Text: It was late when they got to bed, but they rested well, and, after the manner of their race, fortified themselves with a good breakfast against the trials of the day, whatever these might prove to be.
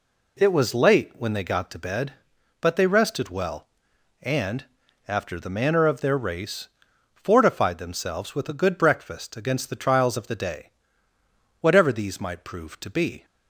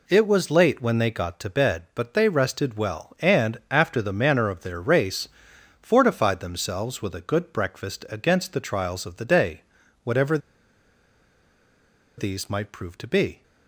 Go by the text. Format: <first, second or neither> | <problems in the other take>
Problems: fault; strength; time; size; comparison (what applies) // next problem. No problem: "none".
first | pauses between "whatever" and "these"; strong; at 10.3 s; 1.7 s long